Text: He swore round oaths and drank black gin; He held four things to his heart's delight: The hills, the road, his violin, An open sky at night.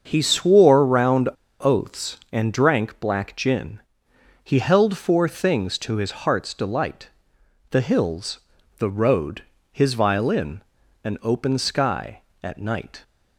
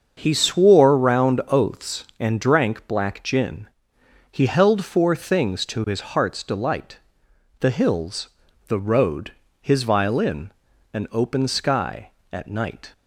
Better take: second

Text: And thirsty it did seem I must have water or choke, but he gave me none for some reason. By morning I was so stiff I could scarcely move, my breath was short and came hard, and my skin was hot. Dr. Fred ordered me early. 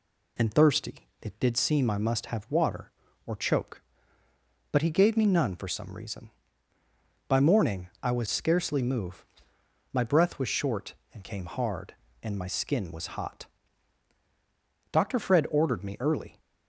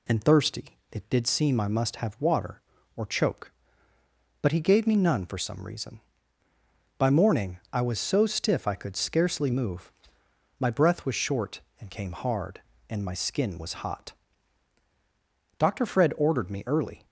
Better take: second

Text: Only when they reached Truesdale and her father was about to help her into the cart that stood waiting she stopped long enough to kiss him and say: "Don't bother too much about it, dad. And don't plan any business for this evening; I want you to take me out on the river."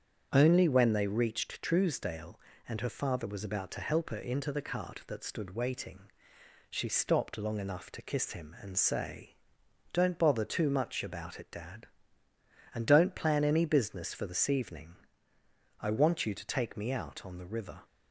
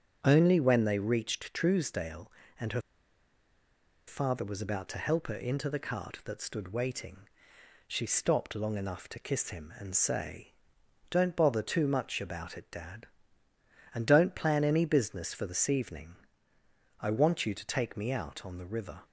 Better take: first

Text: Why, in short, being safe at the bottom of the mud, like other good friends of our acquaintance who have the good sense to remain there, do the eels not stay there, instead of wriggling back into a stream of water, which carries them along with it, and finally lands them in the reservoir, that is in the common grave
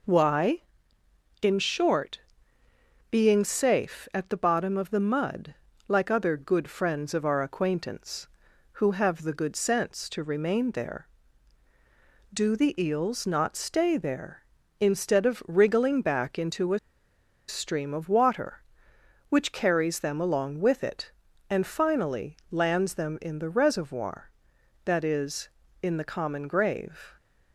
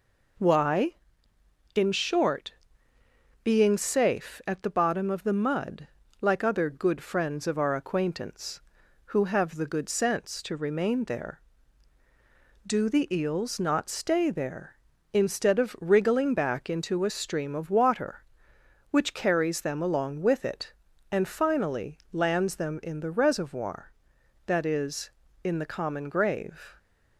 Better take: second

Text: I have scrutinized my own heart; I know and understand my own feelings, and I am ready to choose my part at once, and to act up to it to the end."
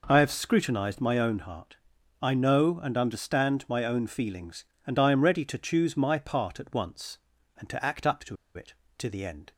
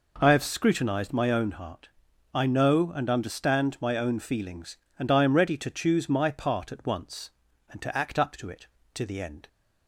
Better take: second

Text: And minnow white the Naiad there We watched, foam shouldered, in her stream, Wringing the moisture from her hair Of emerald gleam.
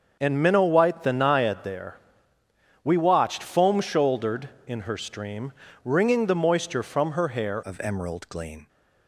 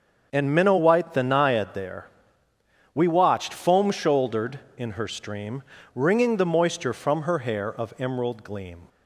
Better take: second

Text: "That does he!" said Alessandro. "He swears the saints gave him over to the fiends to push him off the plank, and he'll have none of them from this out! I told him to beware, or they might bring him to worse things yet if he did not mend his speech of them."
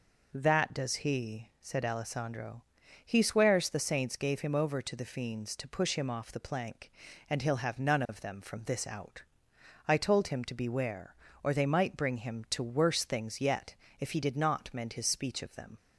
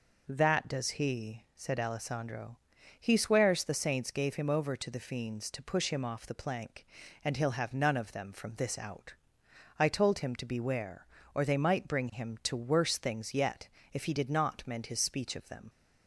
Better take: neither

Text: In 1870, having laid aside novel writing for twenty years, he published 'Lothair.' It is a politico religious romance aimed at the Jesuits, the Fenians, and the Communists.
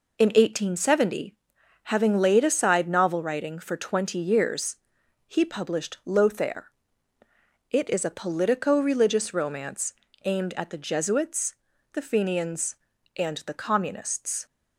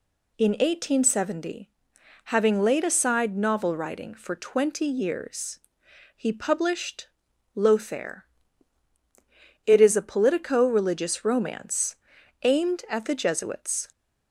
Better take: first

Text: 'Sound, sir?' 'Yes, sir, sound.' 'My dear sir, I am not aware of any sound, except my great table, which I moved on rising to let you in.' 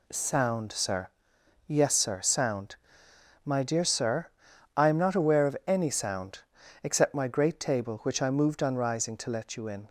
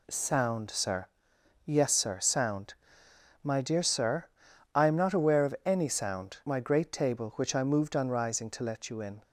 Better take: first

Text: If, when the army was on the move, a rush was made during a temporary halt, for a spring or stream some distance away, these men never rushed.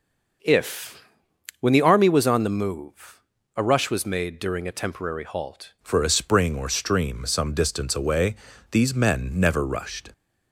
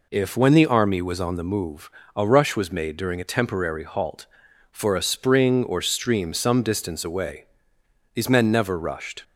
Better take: second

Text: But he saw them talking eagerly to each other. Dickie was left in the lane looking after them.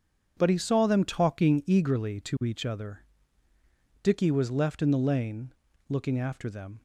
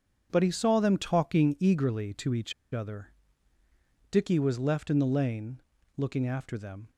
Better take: first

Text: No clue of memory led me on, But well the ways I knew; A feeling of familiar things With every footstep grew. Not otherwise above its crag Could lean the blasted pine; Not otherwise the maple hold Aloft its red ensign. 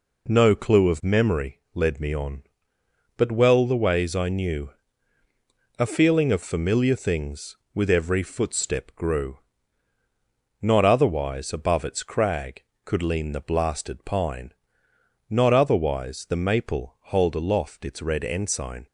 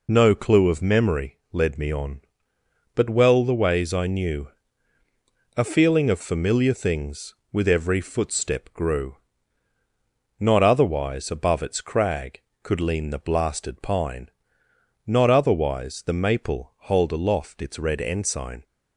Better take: first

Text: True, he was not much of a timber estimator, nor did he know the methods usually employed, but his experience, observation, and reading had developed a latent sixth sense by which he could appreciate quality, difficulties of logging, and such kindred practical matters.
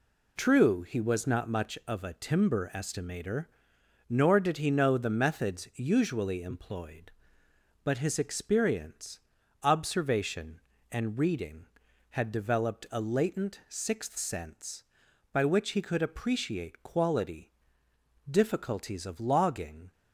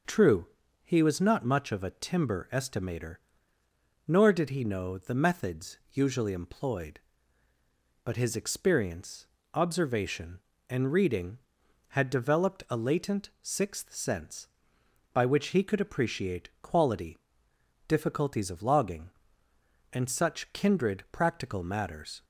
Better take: second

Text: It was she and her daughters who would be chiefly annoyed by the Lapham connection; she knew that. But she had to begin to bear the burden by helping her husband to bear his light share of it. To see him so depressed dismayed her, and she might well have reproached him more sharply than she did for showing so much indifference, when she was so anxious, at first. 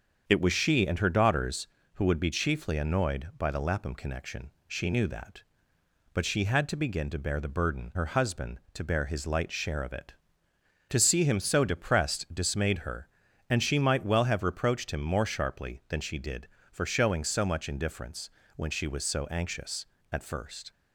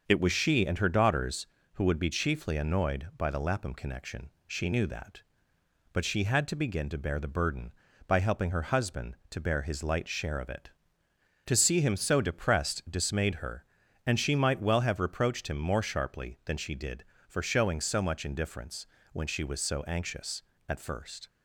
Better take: second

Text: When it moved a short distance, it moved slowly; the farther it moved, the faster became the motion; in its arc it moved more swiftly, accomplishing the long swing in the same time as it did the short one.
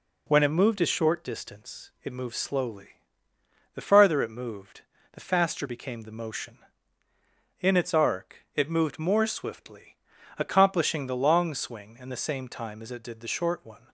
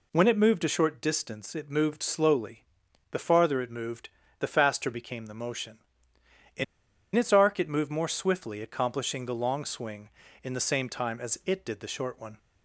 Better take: first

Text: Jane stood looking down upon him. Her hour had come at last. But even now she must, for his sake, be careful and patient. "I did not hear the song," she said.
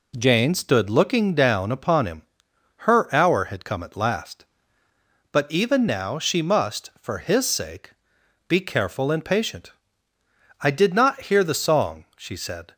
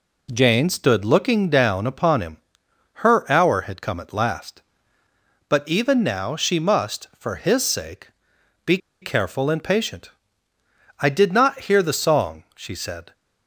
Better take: first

